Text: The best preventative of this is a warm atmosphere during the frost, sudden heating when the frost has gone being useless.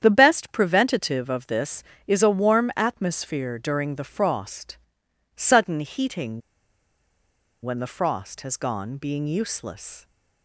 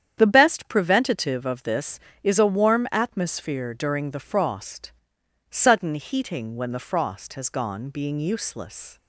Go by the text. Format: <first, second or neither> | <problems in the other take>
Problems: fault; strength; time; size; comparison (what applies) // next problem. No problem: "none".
second | starts louder than the rest; strong; until 1.0 s; 9 dB; strong in the second // pauses between "heating" and "when"; at 6.4 s; 1.2 s long